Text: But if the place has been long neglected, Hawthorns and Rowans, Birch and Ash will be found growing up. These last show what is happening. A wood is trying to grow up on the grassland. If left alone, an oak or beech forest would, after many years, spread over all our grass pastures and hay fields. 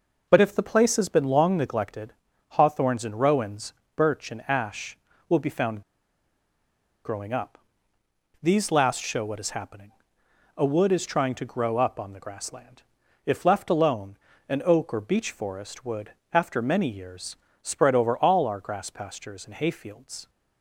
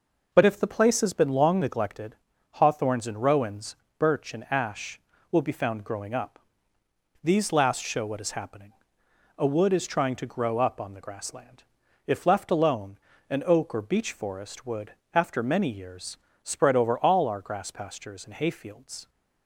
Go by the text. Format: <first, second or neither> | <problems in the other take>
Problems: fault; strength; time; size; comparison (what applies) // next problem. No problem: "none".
second | pauses between "found" and "growing"; at 5.8 s; 1.2 s long